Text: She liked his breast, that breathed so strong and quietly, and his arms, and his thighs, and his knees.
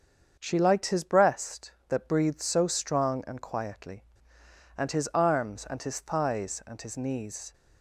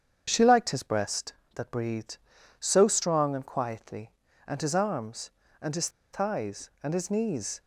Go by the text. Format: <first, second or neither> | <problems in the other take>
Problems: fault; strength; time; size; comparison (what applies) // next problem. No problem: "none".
first | starts louder than the rest; strong; until 1.2 s; 8 dB; also in the first // pauses between "his" and "thighs"; slight; at 5.8 s; 0.24 s long